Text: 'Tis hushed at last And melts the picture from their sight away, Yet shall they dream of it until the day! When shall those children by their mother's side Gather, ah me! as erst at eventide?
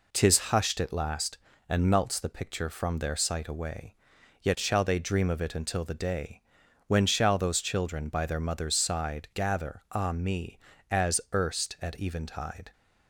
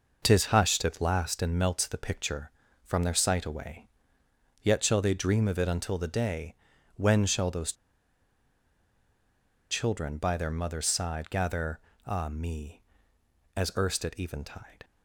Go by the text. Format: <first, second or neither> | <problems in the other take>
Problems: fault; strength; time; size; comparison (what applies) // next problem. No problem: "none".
first | pauses between "those" and "children"; strong; at 7.7 s; 1.9 s long